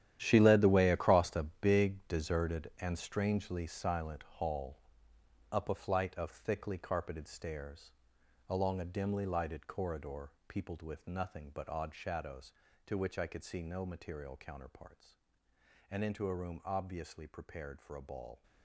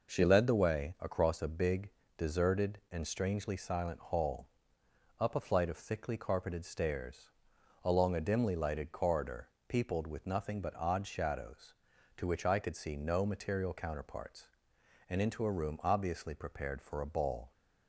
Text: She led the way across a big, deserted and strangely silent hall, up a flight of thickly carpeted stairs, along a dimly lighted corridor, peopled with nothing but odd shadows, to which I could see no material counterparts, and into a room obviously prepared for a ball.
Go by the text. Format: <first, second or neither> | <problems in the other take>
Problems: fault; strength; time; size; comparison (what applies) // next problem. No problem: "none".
second | gets quieter; strong; throughout; 12.5 dB